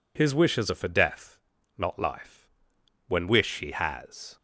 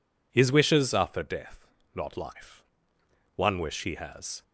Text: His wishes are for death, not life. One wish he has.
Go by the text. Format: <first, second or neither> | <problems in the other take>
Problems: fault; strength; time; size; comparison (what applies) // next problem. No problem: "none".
second | says "When" for "One"; at 3.0 s